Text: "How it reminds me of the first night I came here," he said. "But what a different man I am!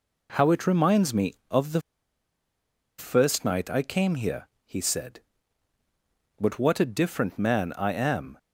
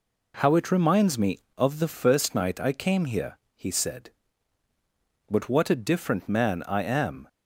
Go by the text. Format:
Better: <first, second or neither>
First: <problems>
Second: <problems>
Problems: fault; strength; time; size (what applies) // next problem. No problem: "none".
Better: second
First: pauses between "the" and "first"; at 1.8 s; 1.1 s long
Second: none